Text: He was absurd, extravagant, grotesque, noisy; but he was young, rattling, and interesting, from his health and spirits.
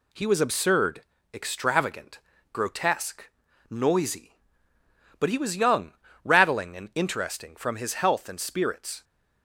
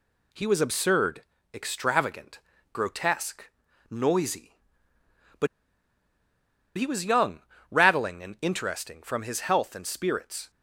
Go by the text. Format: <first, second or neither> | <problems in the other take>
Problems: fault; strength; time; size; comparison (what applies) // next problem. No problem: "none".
first | pauses between "but" and "he"; strong; at 5.4 s; 1.3 s long